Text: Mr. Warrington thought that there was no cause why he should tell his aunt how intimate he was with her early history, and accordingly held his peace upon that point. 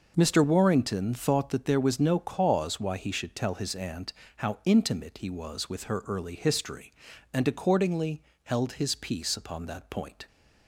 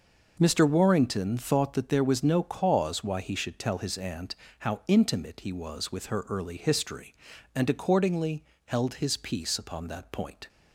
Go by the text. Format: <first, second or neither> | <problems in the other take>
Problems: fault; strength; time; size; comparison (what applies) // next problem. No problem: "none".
neither | pauses between "aunt" and "how"; slight; the same in both // pauses between "accordingly" and "held"; slight; the same in both